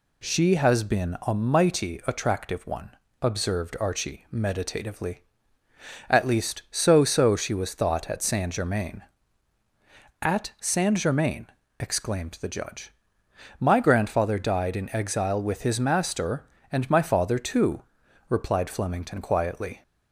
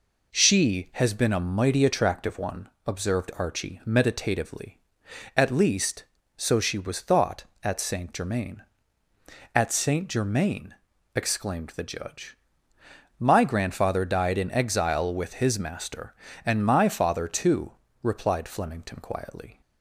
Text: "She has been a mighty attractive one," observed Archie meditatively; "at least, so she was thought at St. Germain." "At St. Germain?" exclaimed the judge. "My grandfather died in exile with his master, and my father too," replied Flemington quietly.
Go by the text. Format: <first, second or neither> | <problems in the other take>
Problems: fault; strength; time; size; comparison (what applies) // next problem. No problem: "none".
second | says "so" twice; at 7.0 s